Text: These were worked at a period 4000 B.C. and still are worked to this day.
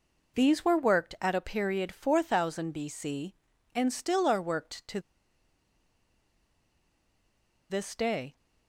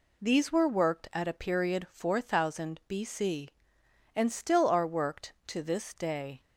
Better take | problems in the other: second | pauses between "to" and "this"; strong; at 4.9 s; 2.7 s long

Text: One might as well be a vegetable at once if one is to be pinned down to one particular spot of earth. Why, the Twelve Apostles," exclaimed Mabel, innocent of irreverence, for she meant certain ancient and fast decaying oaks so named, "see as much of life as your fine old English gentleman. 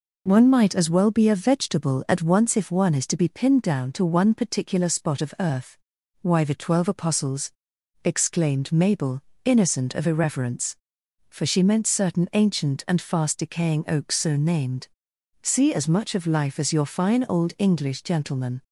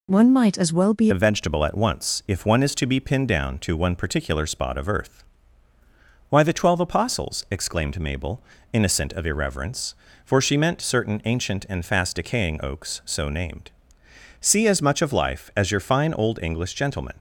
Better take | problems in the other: first | changes voice at "a"; from 1.1 s on; 16.0 s long

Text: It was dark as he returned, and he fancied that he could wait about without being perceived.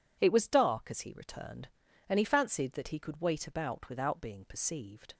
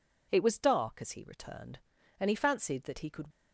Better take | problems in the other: first | stops before "wait about without being perceived"; at 3.3 s

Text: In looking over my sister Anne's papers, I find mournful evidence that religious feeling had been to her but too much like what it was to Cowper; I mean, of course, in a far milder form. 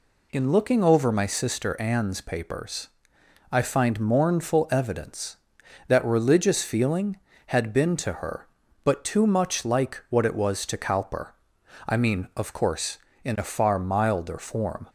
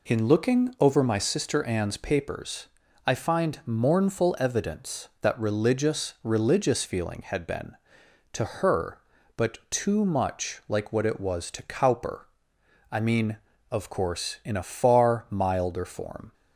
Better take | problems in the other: first | says "religious" twice; at 6.2 s

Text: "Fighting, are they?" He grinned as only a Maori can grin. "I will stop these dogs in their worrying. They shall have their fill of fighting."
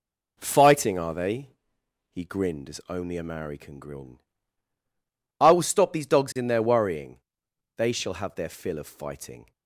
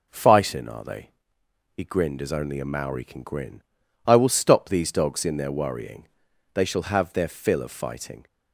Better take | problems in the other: neither | none

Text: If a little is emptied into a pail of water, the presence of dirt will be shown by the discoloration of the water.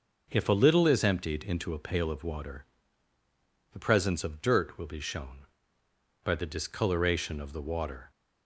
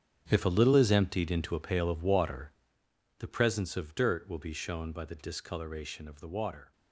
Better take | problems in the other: first | gets quieter; strong; throughout; 13.5 dB

